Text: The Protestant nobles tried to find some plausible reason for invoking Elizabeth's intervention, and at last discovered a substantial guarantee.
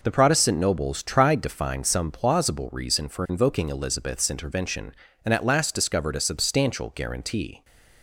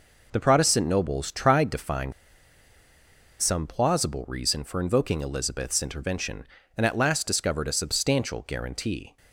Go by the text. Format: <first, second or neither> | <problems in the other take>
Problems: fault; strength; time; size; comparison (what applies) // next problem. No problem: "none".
first | pauses between "find" and "some"; strong; at 2.1 s; 1.2 s long